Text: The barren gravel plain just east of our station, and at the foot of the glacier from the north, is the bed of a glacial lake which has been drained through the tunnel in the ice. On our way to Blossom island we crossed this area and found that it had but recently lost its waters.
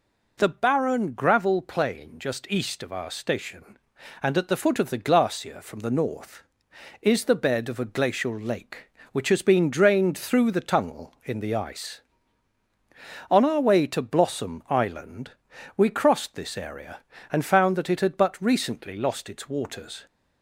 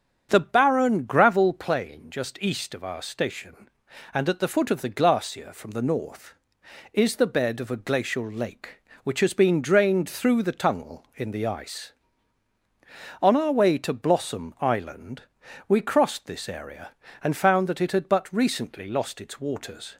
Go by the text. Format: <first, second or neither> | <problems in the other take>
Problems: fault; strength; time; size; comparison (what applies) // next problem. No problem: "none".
first | starts louder than the rest; strong; until 1.7 s; 8 dB // pauses between "island" and "we"; at 15.2 s; 0.44 s long; also in the first